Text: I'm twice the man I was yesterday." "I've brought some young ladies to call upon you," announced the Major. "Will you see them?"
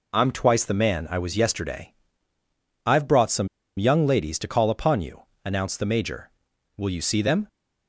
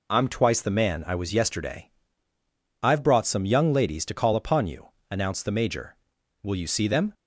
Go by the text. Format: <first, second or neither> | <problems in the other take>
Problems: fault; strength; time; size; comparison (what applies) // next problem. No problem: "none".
second | pauses between "some" and "young"; slight; at 3.4 s; 0.31 s long